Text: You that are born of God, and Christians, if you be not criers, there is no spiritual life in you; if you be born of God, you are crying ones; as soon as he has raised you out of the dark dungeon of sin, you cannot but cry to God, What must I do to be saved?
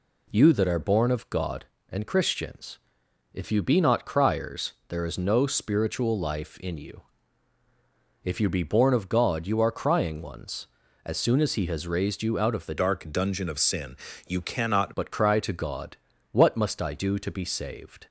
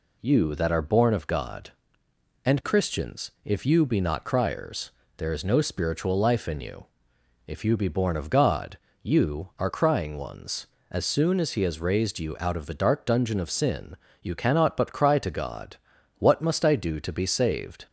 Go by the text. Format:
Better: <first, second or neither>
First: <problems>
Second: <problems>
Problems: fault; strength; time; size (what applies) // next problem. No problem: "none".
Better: second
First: changes voice from "dark" to "cannot"; from 12.7 to 14.9 s; 2.2 s long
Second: none